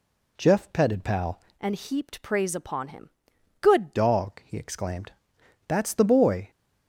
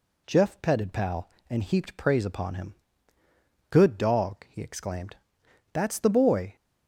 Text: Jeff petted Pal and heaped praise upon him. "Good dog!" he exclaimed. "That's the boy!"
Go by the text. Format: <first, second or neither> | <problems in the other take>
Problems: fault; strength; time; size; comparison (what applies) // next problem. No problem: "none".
second | changes voice from "and" to "Good"; from 1.5 to 3.9 s; 2.4 s long